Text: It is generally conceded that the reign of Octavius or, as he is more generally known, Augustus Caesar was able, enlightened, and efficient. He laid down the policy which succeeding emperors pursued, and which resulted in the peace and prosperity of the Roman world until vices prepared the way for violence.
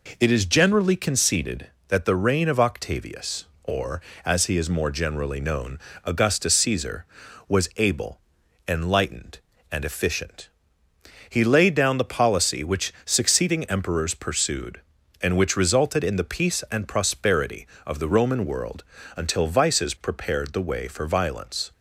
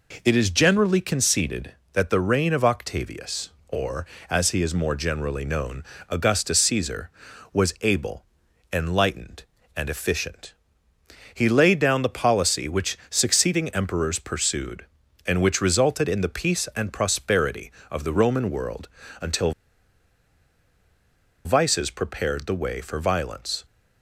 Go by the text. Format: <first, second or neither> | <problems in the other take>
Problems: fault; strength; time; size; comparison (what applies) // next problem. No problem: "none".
first | pauses between "world" and "until"; slight; at 18.8 s; 0.32 s long; slight in the first // pauses between "until" and "vices"; strong; at 19.5 s; 1.9 s long